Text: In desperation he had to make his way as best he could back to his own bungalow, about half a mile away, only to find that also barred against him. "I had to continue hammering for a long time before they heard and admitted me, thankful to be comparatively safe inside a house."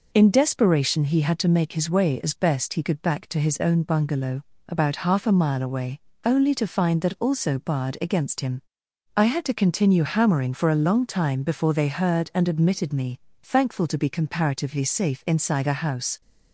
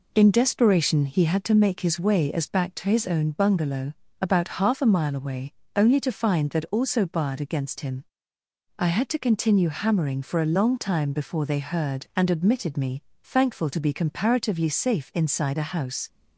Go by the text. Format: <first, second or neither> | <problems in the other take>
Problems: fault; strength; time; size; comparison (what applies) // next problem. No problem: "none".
first | skips "best he could"; at 2.5 s